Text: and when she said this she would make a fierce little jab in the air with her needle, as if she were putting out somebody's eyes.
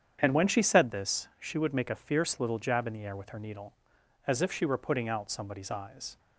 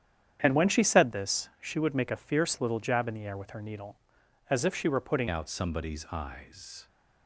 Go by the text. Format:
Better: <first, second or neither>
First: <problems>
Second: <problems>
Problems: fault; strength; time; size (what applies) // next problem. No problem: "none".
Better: first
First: starts louder than the rest; strong; until 1.2 s; 8.5 dB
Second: starts louder than the rest; strong; until 1.4 s; 9 dB // changes voice at "out"; from 5.2 s on; 1.6 s long